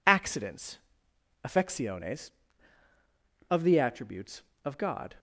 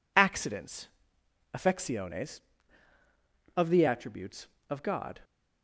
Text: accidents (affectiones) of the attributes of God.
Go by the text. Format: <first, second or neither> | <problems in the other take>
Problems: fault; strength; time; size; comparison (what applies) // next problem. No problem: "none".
neither | none